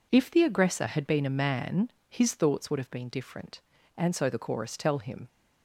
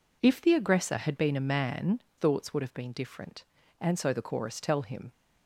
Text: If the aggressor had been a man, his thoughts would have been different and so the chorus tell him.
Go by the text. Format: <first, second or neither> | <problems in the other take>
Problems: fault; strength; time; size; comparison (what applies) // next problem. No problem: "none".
first | skips "his"; at 2.0 s